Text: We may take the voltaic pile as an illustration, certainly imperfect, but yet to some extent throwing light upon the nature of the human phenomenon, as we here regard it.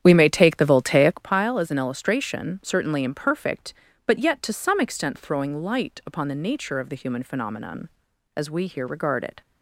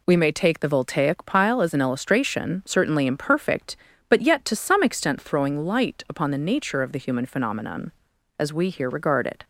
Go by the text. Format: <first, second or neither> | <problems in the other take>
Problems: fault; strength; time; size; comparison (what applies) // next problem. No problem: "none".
second | starts louder than the rest; strong; until 1.3 s; 9.5 dB